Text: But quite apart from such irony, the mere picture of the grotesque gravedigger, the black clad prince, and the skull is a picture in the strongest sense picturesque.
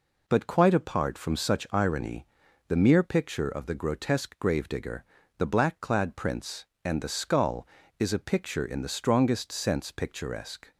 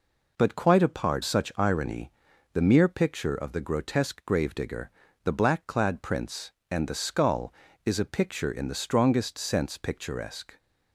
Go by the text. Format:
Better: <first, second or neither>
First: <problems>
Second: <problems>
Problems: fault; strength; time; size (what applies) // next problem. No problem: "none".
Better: first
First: none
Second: skips "from"; at 1.2 s